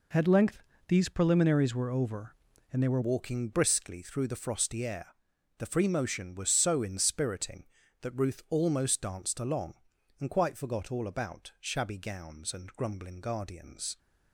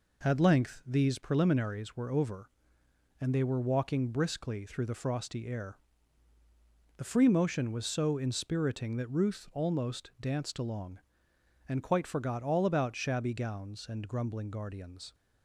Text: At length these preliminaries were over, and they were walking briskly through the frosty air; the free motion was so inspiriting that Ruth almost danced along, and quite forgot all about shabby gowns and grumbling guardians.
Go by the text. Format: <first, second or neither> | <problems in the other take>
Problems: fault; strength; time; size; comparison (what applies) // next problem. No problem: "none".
second | pauses between "length" and "these"; slight; at 0.6 s; 0.28 s long // changes voice at "walking"; from 3.0 s on; 10.9 s long